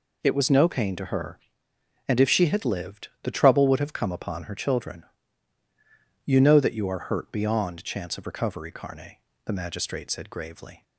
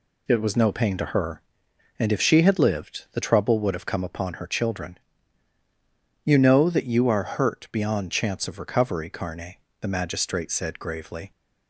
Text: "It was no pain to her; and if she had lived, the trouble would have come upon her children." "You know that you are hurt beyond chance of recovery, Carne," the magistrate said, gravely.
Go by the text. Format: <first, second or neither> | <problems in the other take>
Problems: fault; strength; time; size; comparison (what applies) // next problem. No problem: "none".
neither | none